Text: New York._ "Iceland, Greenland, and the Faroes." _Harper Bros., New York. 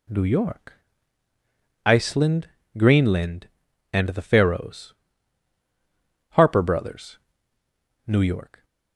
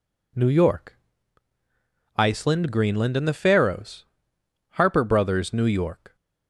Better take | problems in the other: neither | none

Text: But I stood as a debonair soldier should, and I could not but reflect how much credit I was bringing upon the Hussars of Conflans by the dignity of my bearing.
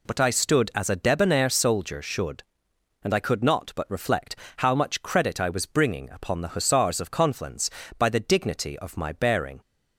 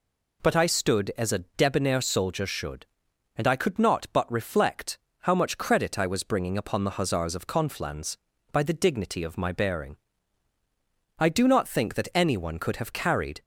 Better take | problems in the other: first | pauses between "reflect" and "how"; slight; at 4.9 s; 0.26 s long; slight in the first // goes on to say "I do not think that anyone could have carried"; strong; from 11.1 s on; 2.2 s long

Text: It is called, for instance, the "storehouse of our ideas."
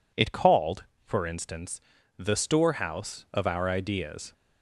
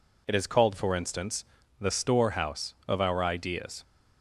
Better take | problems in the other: second | skips "is"; at 0.3 s

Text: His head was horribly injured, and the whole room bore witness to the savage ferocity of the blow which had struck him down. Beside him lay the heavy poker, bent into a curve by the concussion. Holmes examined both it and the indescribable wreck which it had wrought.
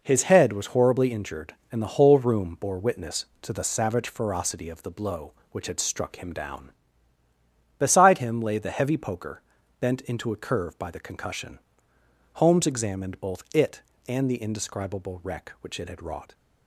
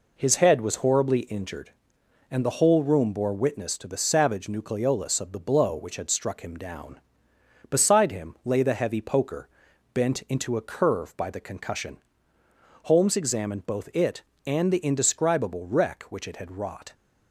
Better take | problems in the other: first | says "nucleolus" for "ferocity"; at 4.4 s

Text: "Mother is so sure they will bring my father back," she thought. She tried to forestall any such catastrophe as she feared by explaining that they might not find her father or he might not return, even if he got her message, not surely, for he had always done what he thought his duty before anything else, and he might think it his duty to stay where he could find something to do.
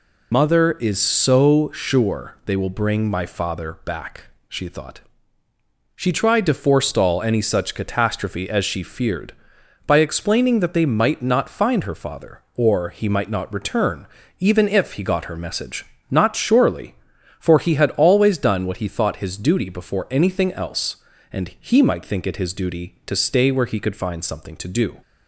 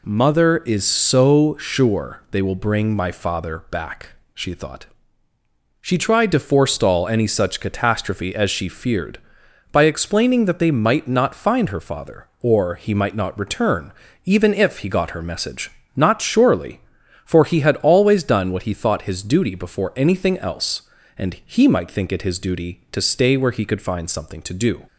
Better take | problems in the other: second | loses the start of "Mother"; at 0.3 s; 135 ms

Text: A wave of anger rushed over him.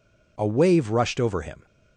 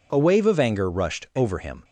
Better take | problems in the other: second | skips "of anger"; at 0.8 s

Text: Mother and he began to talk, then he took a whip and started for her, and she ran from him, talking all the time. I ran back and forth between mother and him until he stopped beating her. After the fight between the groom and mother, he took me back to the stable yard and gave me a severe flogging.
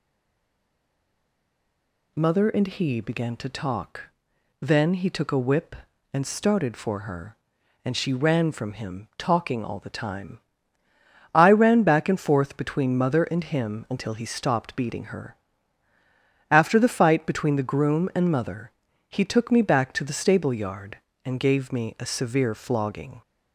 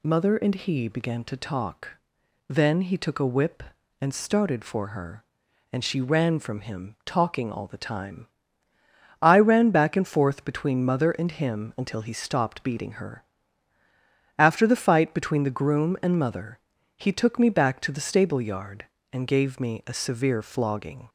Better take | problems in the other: second | stays silent before the first word; until 2.1 s; 2.1 s long

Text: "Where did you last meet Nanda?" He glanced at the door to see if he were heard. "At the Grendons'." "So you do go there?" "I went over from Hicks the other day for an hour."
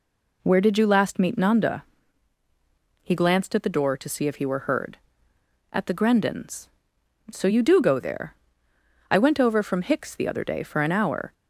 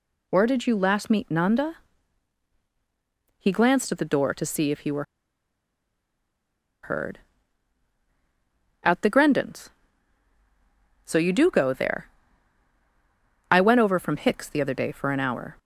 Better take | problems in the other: first | pauses between "were" and "heard"; strong; at 5.0 s; 1.7 s long

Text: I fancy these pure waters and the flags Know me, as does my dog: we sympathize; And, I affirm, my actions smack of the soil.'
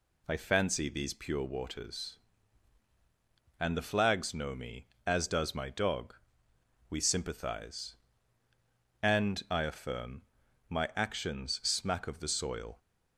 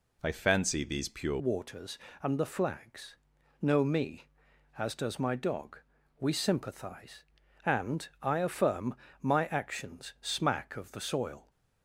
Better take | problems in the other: first | changes voice at "waters"; from 1.3 s on; 10.1 s long // pauses between "flags" and "Know"; at 3.1 s; 0.44 s long

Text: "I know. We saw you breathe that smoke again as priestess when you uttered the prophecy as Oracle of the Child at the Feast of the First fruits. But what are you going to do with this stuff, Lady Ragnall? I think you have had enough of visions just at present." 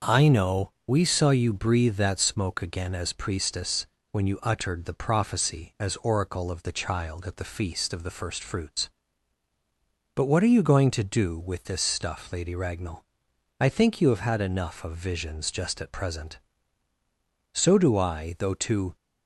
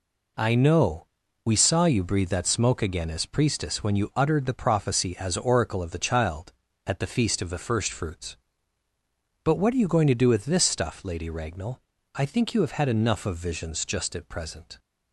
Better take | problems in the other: second | starts louder than the rest; noticeable; until 1.1 s; 6 dB // pauses between "priestess" and "when"; slight; at 3.8 s; 0.24 s long // goes on to say "So do I though to"; from 17.5 s on; 1.4 s long

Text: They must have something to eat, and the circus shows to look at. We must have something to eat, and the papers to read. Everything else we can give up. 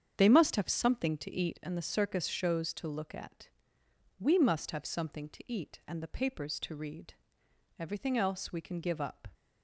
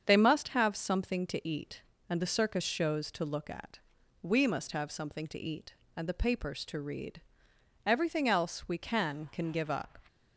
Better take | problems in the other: first | starts louder than the rest; strong; until 1.0 s; 7 dB; strong in the first // says "can" twice; at 9.3 s

